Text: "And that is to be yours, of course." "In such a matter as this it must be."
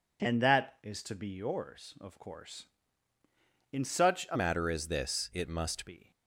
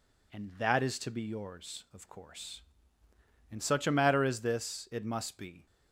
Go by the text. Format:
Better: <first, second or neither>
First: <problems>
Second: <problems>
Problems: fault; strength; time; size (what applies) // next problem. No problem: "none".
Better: second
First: changes voice from "matter" to "must"; from 4.3 to 5.8 s; 1.5 s long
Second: none